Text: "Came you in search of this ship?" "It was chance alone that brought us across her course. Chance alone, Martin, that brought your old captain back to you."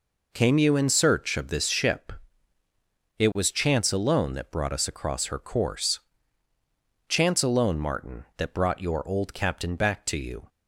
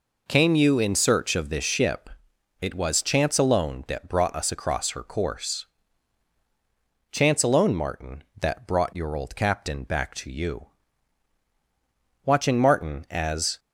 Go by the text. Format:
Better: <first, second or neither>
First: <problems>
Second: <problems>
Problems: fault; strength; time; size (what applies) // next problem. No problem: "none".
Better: first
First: none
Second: goes on to say "Watching Martin as"; from 12.2 s on; 1.3 s long